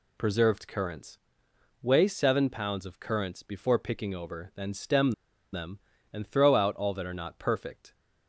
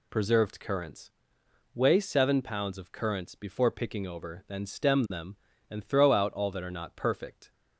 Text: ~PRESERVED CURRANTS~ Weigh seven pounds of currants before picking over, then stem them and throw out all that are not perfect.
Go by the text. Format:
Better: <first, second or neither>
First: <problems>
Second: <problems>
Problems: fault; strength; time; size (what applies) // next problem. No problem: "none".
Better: second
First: pauses between "stem" and "them"; at 5.1 s; 0.39 s long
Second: none